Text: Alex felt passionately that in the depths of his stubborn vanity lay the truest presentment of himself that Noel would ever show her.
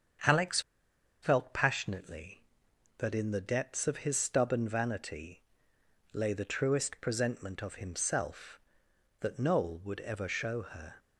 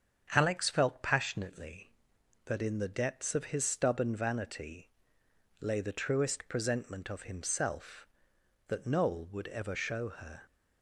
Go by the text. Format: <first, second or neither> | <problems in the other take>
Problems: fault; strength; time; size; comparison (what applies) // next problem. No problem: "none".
second | starts louder than the rest; strong; until 1.8 s; 7.5 dB; strong in the second // pauses between "Alex" and "felt"; noticeable; at 0.5 s; 0.62 s long // pauses between "vanity" and "lay"; noticeable; at 5.4 s; 0.72 s long; noticeable in the second